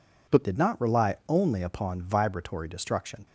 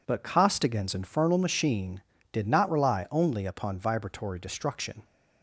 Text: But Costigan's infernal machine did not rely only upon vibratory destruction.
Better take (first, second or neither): second